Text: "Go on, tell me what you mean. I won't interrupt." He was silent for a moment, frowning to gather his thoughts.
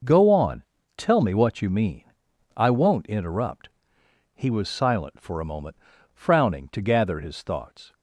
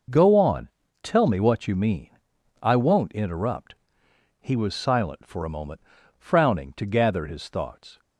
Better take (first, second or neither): neither